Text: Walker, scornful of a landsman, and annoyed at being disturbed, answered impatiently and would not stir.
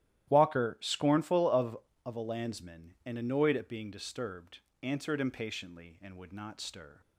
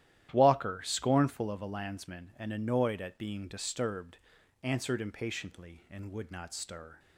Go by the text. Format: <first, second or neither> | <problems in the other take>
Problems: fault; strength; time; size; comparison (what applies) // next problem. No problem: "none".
second | starts louder than the rest; strong; until 1.3 s; 13 dB; strong in the second // says "of" twice; at 2.0 s